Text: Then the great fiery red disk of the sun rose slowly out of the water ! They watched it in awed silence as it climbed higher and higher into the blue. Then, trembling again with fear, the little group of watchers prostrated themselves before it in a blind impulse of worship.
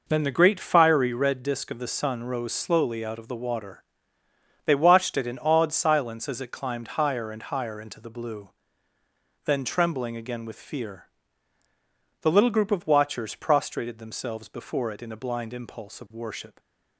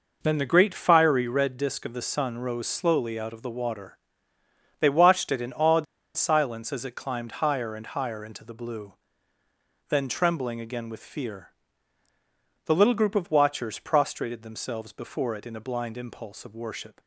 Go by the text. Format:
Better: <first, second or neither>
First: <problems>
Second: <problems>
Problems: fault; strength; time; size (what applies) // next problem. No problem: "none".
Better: first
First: none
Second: pauses between "awed" and "silence"; slight; at 5.8 s; 0.32 s long